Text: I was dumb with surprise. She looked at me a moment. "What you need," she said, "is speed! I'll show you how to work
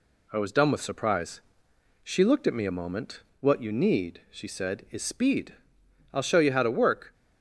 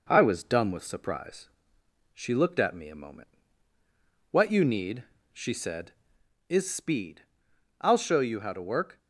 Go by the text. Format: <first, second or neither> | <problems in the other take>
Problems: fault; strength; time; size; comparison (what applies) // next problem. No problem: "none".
neither | none